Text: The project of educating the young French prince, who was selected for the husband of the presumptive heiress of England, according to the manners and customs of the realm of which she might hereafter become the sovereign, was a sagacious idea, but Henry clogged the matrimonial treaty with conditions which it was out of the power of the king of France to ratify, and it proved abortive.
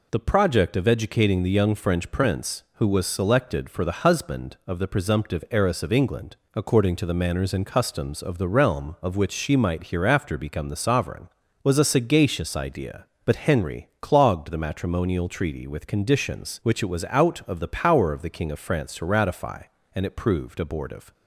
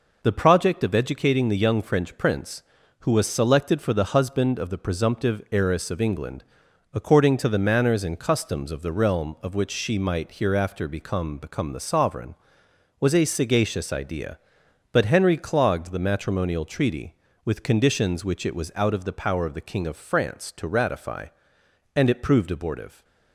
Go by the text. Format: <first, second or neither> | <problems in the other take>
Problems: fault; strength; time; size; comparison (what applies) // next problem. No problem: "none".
first | says "become" twice; at 11.3 s